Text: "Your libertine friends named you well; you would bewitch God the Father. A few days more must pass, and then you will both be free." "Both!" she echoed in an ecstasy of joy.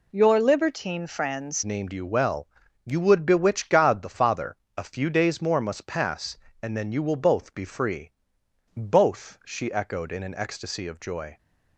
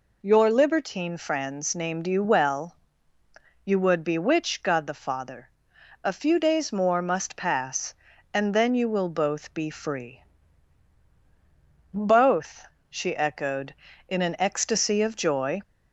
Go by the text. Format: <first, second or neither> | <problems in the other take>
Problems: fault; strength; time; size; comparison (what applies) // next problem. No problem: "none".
second | changes voice at "named"; from 1.6 s on; 9.7 s long